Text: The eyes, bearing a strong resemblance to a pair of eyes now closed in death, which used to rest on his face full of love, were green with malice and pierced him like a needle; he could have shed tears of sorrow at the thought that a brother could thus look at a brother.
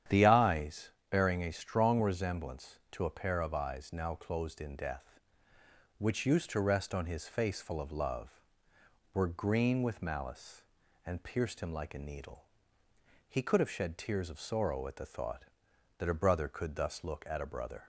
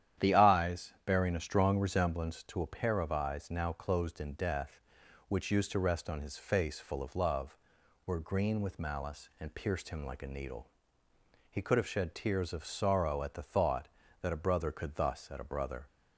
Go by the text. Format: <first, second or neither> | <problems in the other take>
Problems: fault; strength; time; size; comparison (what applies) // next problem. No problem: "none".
first | starts louder than the rest; strong; until 1.3 s; 10.5 dB; strong in the first // skips "look"; at 15.3 s